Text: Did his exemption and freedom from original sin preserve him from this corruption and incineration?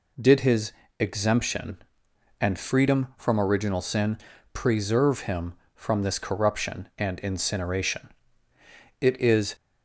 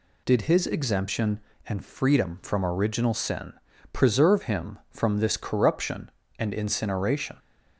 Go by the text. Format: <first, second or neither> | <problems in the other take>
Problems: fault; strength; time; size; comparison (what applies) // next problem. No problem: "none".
second | pauses between "his" and "exemption"; slight; at 0.7 s; 0.28 s long // pauses between "sin" and "preserve"; slight; at 4.1 s; 0.36 s long; also in the second // goes on to say "It is"; from 9.0 s on; 0.54 s long